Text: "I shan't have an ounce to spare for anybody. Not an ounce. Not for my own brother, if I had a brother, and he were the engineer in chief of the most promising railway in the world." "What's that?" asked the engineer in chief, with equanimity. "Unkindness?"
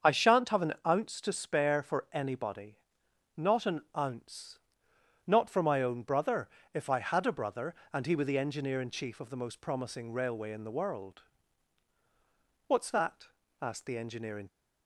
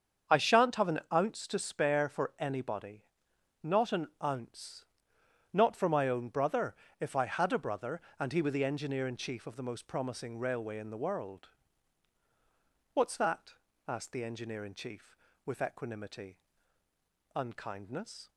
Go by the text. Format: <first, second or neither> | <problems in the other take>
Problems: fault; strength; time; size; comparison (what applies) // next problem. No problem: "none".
second | starts louder than the rest; strong; until 1.1 s; 7 dB; strong in the second // pauses between "an" and "ounce"; slight; at 3.8 s; 0.16 s long; slight in the second // stops before "chief with equanimity Unkindness"; at 14.4 s